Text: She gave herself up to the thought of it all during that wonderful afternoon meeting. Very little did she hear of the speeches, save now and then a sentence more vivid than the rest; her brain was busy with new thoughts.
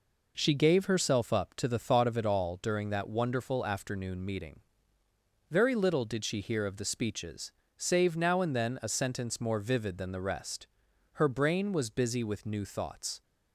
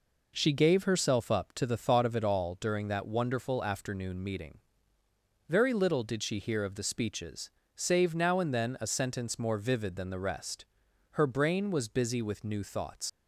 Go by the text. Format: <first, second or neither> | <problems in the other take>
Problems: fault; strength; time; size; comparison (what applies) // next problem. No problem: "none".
first | leaves "thoughts" unfinished; at 13.0 s; 105 ms